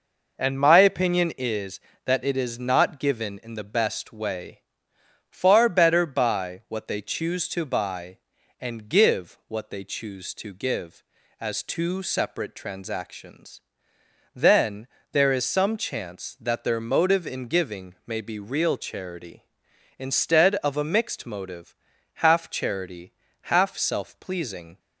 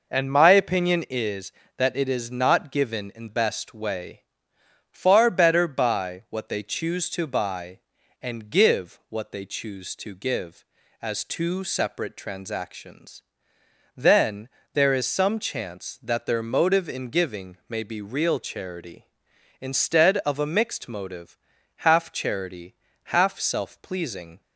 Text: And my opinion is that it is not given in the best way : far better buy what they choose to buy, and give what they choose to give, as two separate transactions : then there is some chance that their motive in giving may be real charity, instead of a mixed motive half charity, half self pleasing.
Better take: first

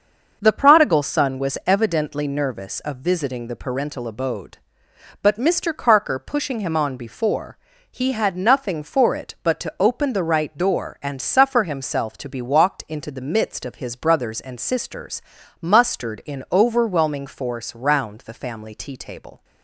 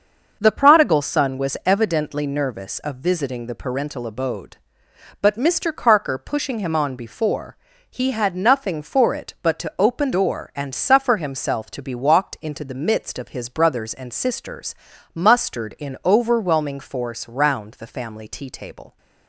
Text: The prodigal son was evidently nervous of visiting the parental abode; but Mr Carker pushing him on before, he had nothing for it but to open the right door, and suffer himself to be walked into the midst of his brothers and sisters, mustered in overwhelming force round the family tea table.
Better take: first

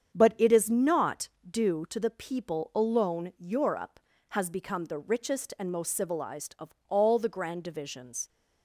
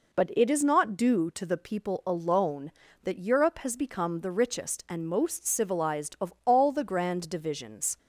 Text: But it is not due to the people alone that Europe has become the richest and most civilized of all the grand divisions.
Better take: second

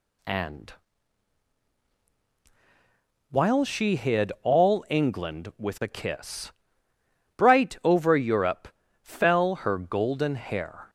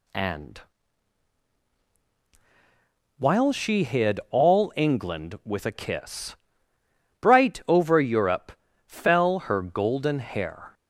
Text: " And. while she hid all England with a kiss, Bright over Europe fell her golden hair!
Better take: neither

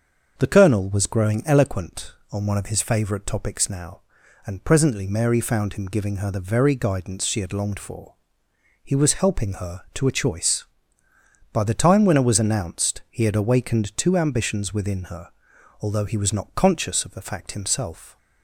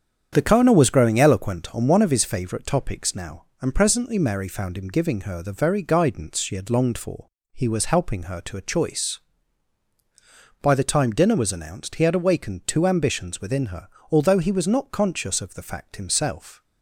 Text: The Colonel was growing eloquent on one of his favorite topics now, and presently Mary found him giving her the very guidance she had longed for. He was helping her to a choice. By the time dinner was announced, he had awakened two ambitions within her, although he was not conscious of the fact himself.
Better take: second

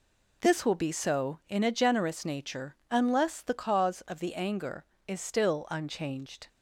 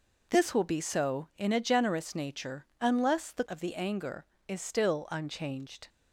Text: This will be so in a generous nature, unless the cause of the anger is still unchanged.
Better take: first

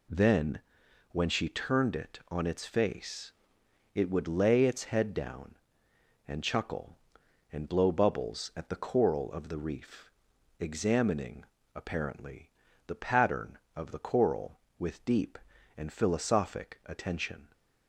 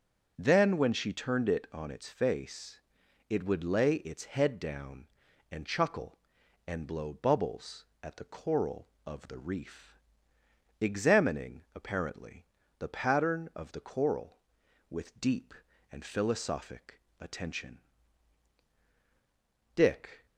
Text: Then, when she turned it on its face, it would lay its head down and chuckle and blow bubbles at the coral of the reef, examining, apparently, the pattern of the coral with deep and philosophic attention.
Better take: first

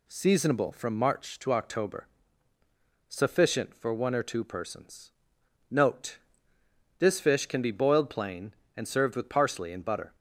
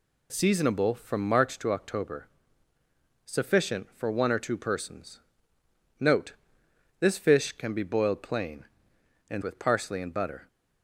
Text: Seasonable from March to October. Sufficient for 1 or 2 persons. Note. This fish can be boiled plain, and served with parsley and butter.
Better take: first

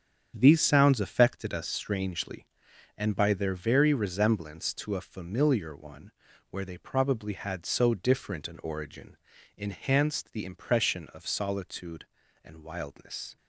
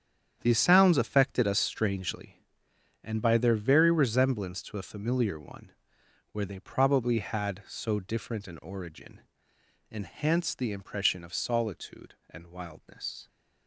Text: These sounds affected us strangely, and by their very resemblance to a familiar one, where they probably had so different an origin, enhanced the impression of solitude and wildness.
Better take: neither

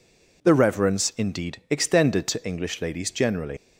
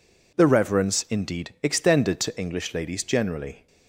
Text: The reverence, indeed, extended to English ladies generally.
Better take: second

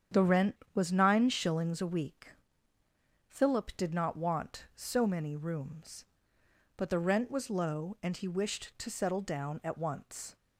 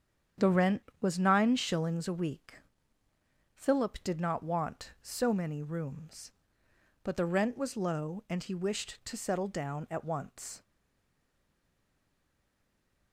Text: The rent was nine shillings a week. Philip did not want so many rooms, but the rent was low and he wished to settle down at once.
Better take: first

